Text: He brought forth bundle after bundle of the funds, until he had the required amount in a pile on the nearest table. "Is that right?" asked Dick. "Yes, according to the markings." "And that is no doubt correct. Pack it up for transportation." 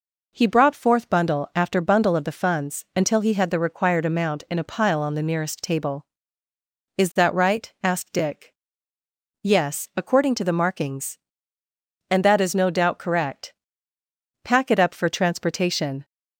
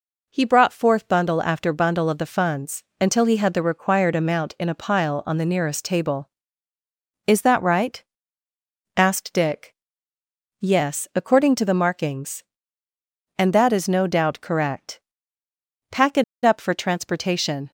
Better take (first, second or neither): first